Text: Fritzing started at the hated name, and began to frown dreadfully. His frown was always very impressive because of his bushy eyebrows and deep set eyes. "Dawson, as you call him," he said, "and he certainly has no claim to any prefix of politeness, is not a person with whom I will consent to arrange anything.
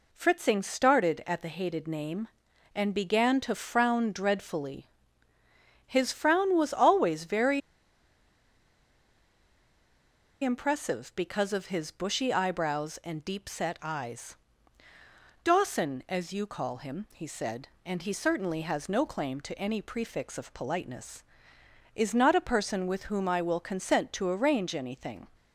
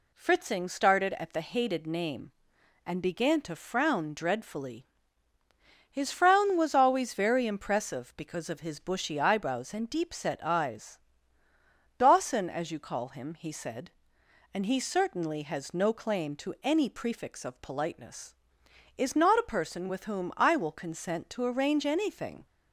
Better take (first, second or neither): second